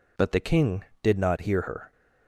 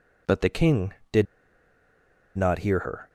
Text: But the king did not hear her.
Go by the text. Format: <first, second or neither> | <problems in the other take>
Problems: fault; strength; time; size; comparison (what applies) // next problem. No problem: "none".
first | pauses between "did" and "not"; at 1.2 s; 1.1 s long